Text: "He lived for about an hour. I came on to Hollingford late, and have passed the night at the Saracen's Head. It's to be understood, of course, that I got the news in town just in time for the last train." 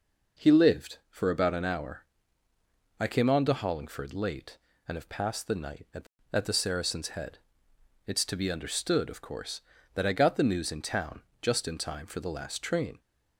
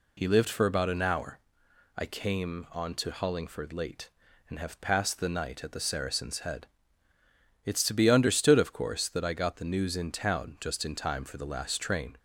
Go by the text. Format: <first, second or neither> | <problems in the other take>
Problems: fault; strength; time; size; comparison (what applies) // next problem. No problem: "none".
second | says "at" twice; at 6.3 s // pauses between "town" and "just"; slight; at 11.2 s; 0.18 s long